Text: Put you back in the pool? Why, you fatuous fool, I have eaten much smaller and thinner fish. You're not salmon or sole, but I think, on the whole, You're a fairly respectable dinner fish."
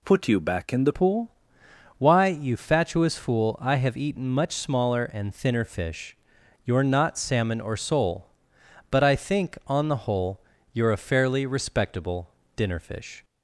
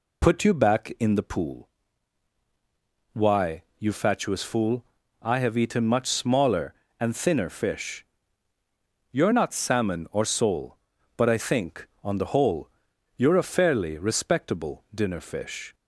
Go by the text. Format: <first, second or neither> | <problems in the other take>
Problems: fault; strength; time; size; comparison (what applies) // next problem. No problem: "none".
second | changes voice at "pool"; from 0.9 s on; 12.3 s long // pauses between "respectable" and "dinner"; slight; at 12.2 s; 0.26 s long